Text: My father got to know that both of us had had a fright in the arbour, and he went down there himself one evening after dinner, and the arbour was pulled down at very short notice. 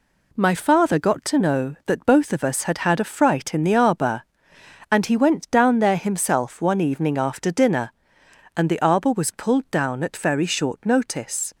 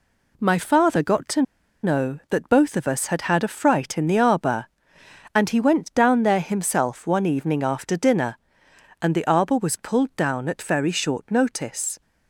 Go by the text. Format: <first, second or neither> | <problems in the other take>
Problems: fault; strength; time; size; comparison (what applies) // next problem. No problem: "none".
first | pauses between "to" and "know"; at 1.4 s; 0.41 s long